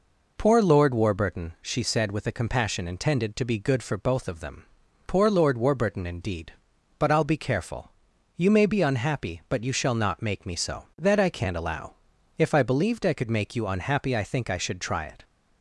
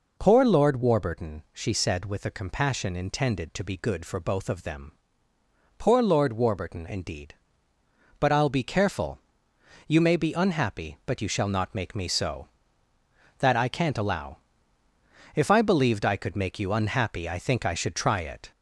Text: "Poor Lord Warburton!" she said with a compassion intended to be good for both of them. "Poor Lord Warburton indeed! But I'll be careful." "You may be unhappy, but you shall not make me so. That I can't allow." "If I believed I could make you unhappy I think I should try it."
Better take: first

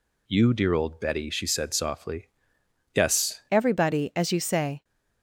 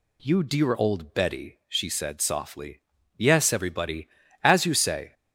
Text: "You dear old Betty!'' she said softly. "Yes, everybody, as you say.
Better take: second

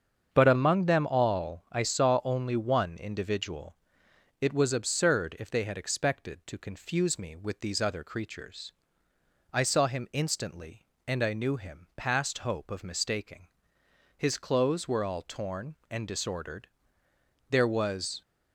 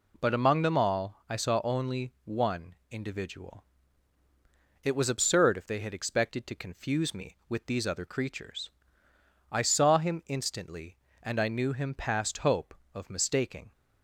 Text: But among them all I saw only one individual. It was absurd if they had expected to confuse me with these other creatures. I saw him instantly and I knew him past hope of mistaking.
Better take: second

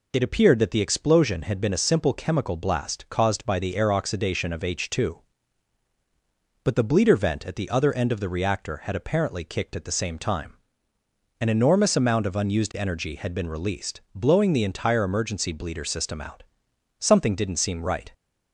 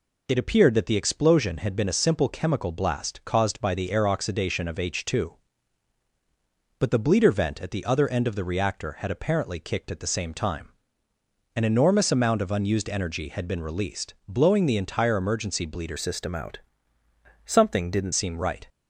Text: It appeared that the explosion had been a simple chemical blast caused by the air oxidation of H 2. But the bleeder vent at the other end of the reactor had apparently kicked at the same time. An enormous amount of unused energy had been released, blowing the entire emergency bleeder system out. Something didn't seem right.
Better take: first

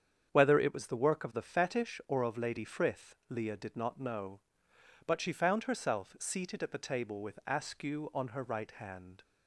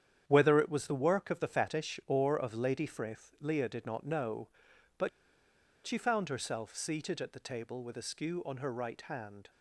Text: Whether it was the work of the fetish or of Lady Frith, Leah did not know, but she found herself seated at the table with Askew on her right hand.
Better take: first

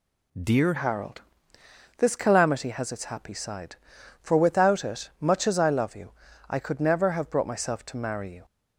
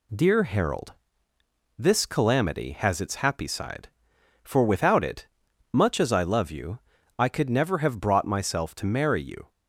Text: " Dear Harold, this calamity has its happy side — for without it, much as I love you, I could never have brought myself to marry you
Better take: second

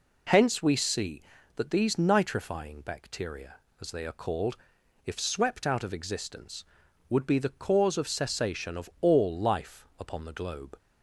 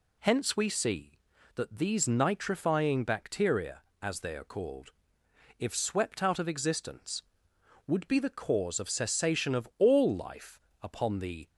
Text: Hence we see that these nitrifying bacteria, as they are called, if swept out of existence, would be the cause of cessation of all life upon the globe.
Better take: first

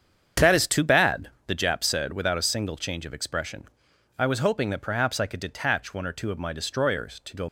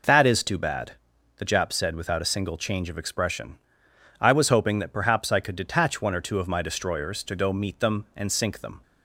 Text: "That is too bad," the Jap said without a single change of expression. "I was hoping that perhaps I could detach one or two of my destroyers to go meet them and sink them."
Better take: second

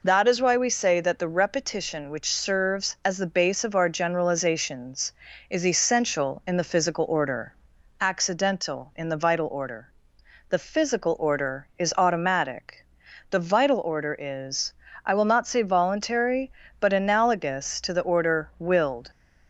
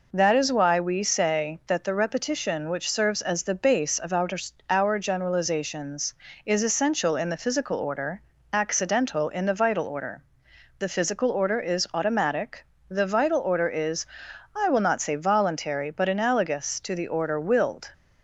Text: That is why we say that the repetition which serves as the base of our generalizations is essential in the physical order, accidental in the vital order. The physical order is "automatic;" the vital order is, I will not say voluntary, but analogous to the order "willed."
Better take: first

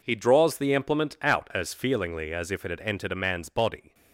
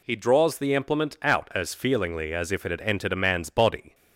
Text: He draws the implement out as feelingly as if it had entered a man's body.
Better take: second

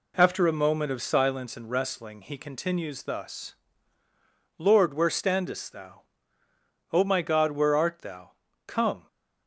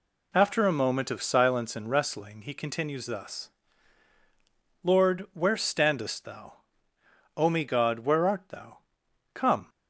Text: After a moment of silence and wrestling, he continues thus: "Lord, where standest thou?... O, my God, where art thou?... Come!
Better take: first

